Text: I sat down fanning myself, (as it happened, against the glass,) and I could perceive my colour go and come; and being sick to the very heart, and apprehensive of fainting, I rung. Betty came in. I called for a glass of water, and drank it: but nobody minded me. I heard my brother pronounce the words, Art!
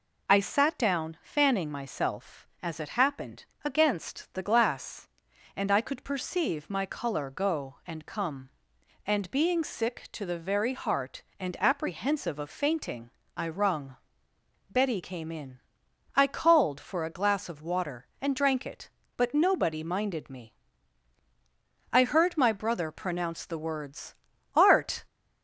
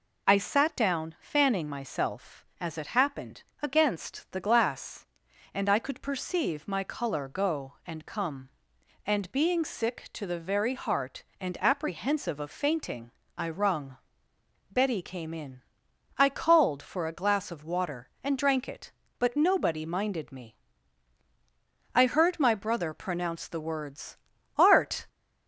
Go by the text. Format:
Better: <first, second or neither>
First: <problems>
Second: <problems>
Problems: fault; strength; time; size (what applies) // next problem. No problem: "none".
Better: neither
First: none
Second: none